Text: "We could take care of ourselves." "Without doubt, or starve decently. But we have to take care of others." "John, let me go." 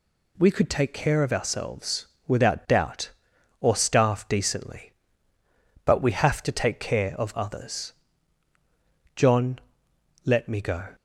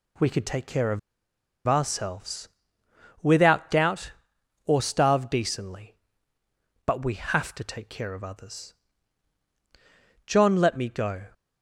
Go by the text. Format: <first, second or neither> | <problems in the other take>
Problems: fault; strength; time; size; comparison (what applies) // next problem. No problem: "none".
first | pauses between "of" and "ourselves"; noticeable; at 0.9 s; 0.68 s long